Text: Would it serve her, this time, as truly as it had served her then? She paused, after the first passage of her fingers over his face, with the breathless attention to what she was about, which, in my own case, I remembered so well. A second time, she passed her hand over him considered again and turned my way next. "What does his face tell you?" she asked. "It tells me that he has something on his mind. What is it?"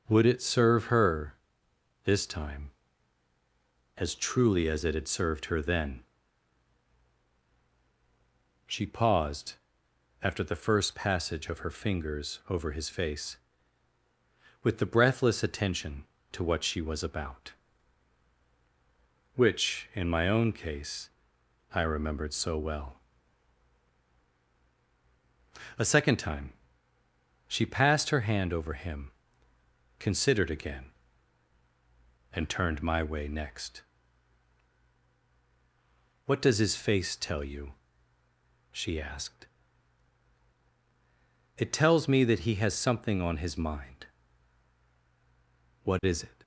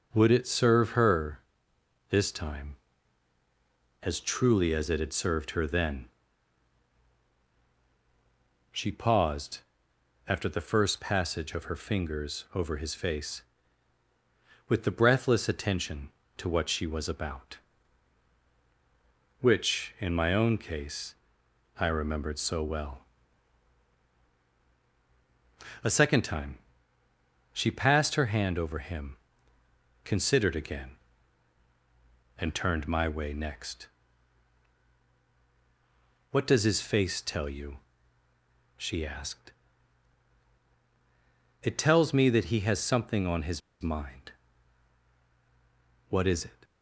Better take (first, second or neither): first